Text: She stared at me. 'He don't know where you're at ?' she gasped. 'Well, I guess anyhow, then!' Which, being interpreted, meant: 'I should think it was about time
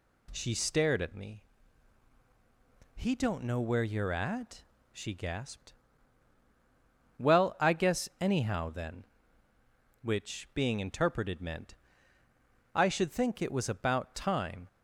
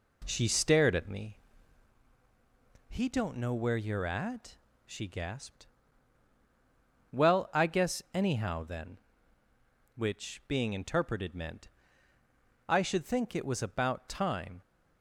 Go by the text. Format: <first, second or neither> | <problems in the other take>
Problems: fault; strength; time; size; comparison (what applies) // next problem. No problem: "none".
first | starts louder than the rest; until 1.9 s; 3.5 dB